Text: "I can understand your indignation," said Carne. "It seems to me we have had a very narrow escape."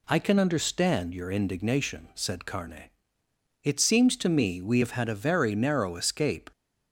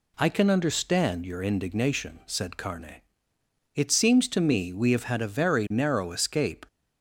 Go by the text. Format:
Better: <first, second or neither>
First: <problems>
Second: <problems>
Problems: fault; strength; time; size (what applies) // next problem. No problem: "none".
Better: neither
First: none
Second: none